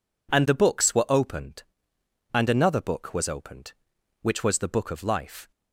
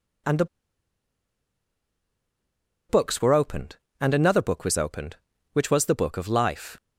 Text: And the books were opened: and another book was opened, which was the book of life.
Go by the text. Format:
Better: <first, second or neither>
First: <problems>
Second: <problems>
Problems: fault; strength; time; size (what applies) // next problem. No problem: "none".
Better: first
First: none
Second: pauses between "the" and "books"; strong; at 0.4 s; 2.4 s long